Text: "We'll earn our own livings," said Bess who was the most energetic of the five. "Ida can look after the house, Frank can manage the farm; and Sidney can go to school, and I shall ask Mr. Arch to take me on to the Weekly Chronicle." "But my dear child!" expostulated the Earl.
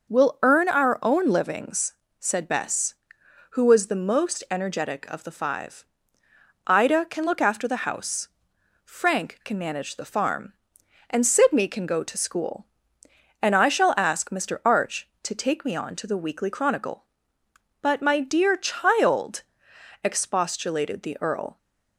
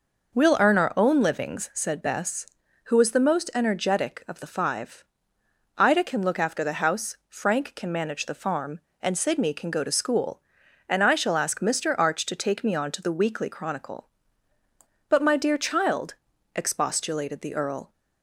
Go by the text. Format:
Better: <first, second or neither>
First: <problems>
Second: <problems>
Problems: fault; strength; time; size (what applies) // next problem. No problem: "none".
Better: neither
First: none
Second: none